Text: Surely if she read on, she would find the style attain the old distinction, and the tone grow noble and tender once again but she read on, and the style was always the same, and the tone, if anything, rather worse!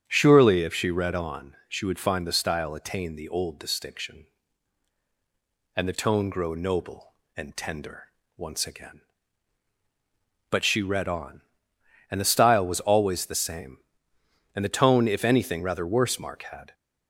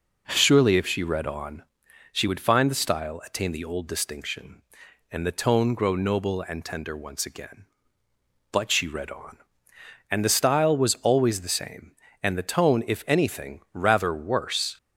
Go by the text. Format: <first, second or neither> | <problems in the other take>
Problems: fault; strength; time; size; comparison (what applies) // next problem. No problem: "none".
second | starts louder than the rest; strong; until 1.0 s; 8 dB // pauses between "tender" and "once"; slight; at 8.0 s; 0.30 s long // goes on to say "Mark had"; from 16.1 s on; 0.54 s long